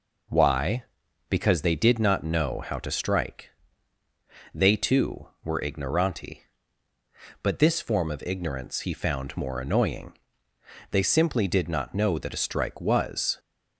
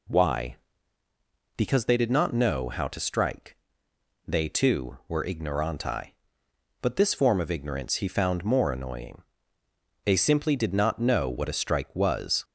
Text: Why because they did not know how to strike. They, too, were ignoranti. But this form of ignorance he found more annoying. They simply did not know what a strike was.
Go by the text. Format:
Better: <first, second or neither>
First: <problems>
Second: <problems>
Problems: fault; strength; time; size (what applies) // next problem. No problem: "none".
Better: second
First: says "that" for "what"; at 12.1 s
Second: none